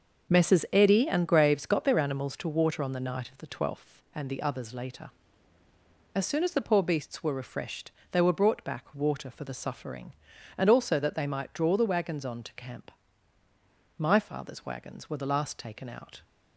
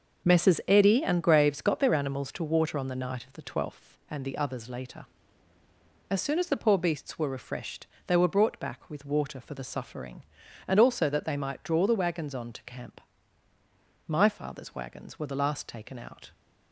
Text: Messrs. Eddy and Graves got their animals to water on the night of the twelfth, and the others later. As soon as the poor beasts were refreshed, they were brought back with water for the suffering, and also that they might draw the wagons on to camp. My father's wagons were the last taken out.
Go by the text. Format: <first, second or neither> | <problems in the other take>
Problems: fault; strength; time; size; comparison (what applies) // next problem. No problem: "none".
second | starts louder than the rest; until 1.3 s; 7 dB; also in the second // skips "with"; at 8.9 s